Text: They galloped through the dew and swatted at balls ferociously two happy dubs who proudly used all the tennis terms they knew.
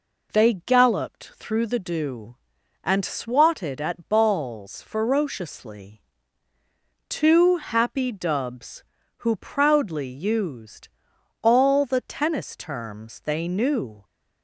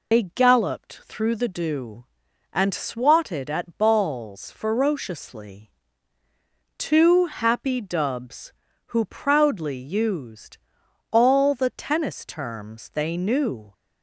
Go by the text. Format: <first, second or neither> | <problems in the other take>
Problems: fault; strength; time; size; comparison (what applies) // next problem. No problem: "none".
first | loses the start of "They"; at 0.1 s; 105 ms // pauses between "ferociously" and "two"; at 5.7 s; 1.0 s long; also in the first // pauses between "used" and "all"; noticeable; at 10.5 s; 0.54 s long; noticeable in the first